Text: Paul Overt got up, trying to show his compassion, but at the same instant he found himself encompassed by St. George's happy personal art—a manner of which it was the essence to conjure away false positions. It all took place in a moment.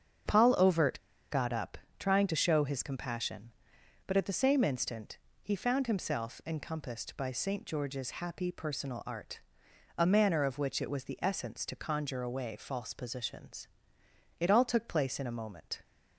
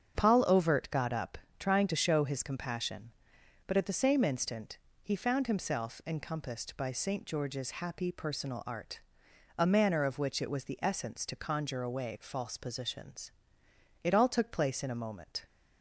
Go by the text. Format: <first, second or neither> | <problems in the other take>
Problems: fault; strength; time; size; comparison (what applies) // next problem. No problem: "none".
second | starts louder than the rest; strong; until 1.5 s; 7.5 dB; strong in the second // pauses between "Overt" and "got"; slight; at 1.0 s; 0.29 s long // pauses between "instant" and "he"; slight; at 5.1 s; 0.24 s long; slight in the second